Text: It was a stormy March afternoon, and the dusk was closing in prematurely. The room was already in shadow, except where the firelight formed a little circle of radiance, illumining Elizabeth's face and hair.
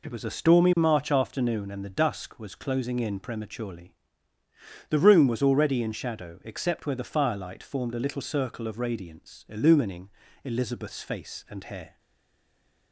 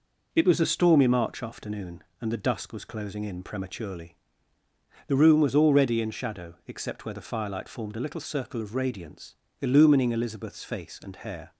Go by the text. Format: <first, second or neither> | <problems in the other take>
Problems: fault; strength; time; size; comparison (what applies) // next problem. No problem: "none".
second | pauses between "illumining" and "Elizabeth's"; at 10.0 s; 0.38 s long // stays silent after the last word; from 11.9 s on; 1.0 s long